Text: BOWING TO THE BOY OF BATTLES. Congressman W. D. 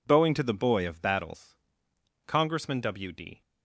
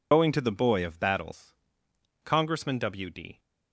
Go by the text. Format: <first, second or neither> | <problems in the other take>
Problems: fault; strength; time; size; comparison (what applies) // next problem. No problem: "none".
first | loses the start of "BOWING"; at 0.1 s; 65 ms